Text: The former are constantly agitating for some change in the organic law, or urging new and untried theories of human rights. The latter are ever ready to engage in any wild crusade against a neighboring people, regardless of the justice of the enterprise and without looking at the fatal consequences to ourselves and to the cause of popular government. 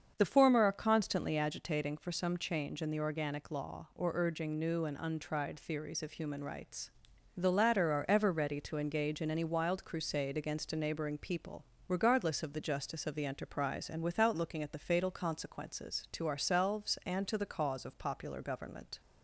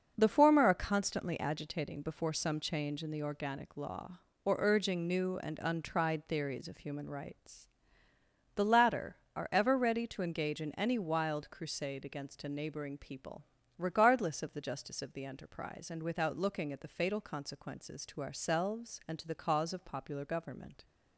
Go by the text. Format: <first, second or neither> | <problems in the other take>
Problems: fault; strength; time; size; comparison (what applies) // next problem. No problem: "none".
first | starts louder than the rest; until 1.1 s; 6 dB; also in the first // says "before" for "for"; at 2.0 s